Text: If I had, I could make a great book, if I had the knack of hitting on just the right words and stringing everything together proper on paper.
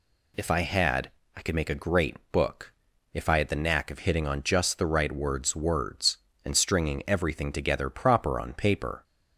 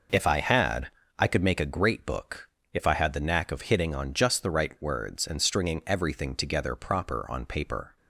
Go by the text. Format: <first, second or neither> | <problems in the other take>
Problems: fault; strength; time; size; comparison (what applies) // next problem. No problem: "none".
second | pauses between "great" and "book"; slight; at 2.1 s; 0.16 s long // says "words" twice; at 5.5 s